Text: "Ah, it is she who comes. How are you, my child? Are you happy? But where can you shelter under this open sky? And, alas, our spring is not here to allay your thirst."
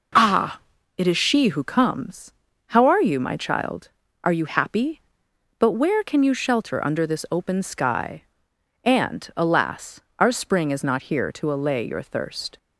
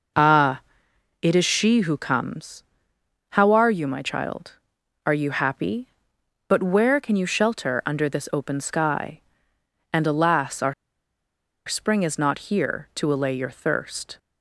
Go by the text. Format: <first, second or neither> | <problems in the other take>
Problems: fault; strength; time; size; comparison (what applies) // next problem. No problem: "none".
first | pauses between "our" and "spring"; noticeable; at 10.7 s; 0.94 s long